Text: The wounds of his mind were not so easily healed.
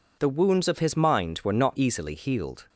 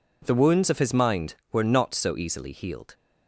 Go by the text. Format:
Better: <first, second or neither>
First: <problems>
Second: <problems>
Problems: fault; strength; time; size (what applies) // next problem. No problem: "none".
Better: second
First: skips "so"; at 1.7 s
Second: none